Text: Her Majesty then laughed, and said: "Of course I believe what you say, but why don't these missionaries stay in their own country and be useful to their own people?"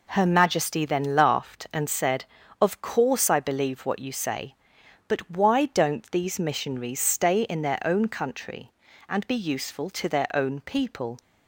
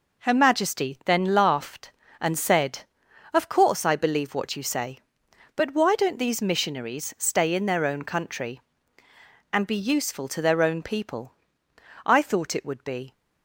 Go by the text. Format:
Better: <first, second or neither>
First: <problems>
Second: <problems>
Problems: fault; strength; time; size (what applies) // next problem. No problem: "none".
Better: first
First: none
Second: goes on to say "I thought it would be"; noticeable; from 12.0 s on; 1.0 s long